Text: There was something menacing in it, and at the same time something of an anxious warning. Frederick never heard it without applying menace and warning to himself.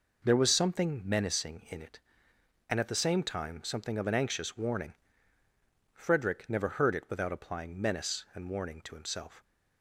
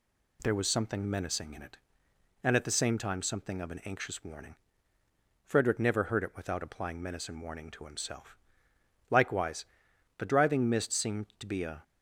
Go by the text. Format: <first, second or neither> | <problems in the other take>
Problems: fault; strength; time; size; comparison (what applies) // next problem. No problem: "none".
first | goes on to say "Likewise the driving mist seemed to be a"; strong; from 9.1 s on; 2.7 s long